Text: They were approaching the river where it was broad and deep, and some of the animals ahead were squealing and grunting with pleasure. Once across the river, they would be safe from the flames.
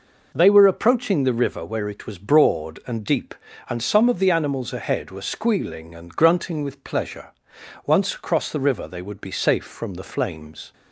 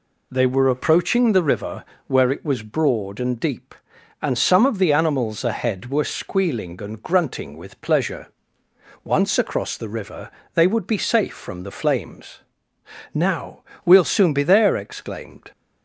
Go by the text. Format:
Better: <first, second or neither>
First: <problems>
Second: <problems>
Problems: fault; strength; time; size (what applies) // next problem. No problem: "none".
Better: first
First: none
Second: pauses between "river" and "where"; slight; at 1.8 s; 0.22 s long // goes on to say "Now we'll soon be there exclaimed"; strong; from 13.1 s on; 2.3 s long